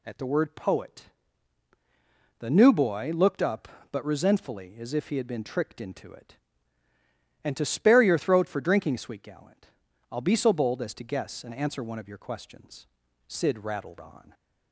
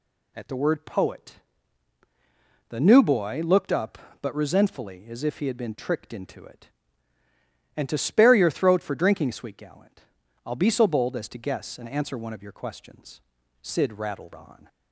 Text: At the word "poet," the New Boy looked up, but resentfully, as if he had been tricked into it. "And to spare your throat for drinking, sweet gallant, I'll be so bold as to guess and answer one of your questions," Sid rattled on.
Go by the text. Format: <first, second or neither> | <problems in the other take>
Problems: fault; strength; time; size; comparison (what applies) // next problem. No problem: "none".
neither | none